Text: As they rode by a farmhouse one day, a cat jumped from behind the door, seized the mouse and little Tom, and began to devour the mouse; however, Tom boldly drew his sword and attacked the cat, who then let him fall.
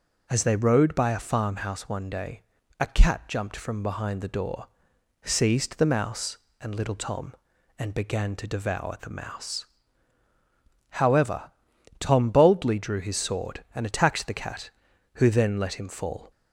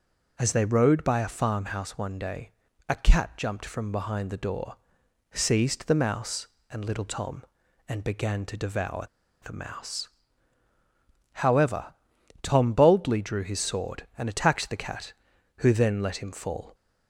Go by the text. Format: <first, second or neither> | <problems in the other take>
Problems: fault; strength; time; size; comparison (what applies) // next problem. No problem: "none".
first | pauses between "devour" and "the"; at 9.0 s; 0.37 s long